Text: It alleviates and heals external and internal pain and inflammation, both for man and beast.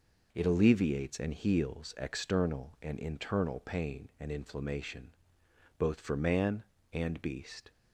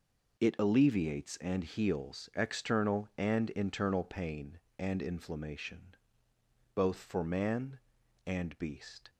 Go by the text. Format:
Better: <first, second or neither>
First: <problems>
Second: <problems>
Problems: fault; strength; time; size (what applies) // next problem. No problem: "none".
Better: neither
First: none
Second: none